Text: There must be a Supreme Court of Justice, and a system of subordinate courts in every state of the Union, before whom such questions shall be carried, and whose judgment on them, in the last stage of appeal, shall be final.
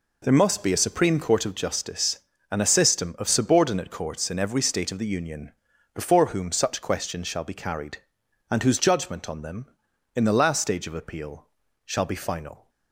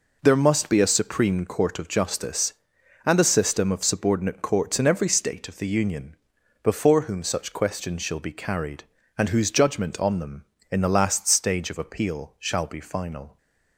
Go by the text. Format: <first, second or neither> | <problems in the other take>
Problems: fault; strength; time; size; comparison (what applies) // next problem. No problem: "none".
neither | none